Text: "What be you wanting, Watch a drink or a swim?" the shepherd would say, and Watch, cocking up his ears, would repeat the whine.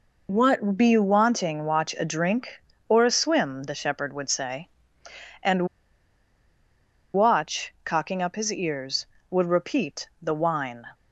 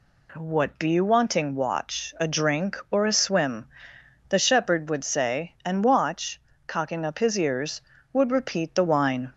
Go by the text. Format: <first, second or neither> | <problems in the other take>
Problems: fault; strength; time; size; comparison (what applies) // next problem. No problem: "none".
second | pauses between "and" and "Watch"; strong; at 5.6 s; 1.4 s long